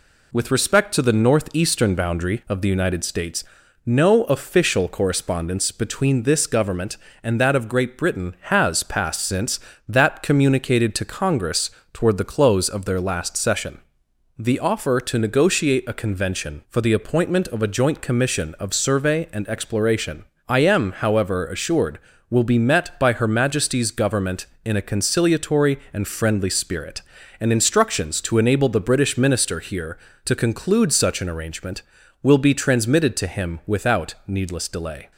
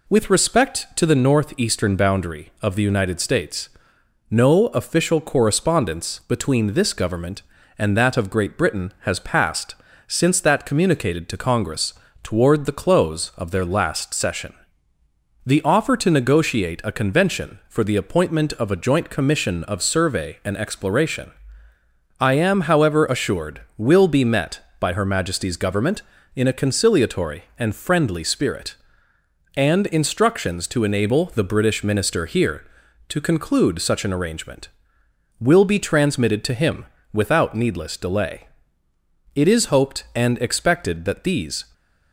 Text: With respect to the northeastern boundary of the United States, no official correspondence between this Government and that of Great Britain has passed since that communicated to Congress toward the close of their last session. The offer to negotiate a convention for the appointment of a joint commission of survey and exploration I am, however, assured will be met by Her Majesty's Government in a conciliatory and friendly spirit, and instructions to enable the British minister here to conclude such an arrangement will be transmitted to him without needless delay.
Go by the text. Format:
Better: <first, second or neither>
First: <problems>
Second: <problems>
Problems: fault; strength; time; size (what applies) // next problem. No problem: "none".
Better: first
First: pauses between "Congress" and "toward"; slight; at 11.6 s; 0.24 s long // pauses between "exploration" and "I"; slight; at 20.2 s; 0.24 s long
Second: pauses between "passed" and "since"; slight; at 9.7 s; 0.30 s long // pauses between "Congress" and "toward"; slight; at 11.9 s; 0.32 s long // pauses between "exploration" and "I"; noticeable; at 21.3 s; 0.88 s long // pauses between "him" and "without"; slight; at 36.8 s; 0.26 s long // goes on to say "It is hoped and expected that these"; strong; from 39.3 s on; 2.3 s long